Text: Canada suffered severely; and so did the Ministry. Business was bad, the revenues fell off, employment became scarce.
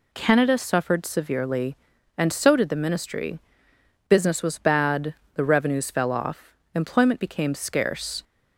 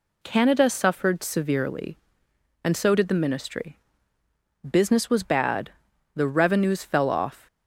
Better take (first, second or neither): first